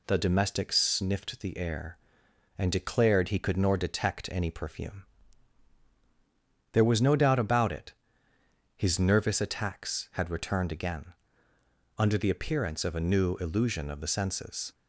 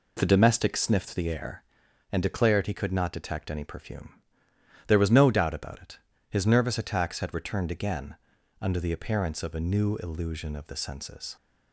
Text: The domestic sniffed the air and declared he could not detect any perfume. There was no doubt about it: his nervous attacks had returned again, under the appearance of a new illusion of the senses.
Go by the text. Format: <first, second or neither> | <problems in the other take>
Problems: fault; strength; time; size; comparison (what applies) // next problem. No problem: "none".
second | says "nor" for "not"; at 3.5 s